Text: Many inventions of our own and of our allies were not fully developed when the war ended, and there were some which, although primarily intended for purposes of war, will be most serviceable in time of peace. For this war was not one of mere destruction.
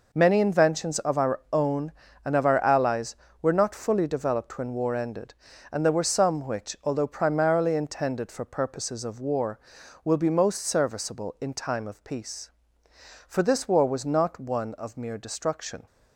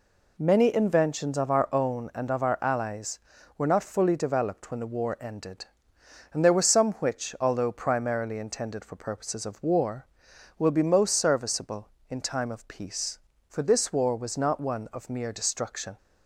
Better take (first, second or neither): second